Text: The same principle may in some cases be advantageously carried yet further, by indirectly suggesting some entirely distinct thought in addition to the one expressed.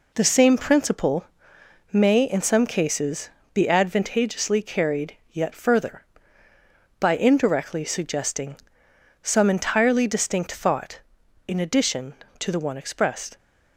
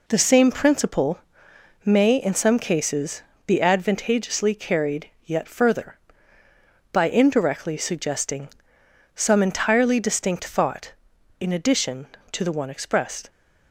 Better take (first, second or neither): neither